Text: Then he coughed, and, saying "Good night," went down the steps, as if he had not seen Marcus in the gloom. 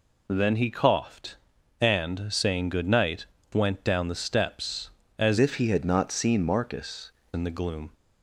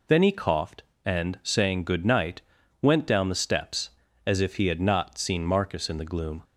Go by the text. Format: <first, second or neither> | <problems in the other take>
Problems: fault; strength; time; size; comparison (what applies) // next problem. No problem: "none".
second | changes voice from "if" to "Marcus"; from 5.3 to 7.0 s; 1.7 s long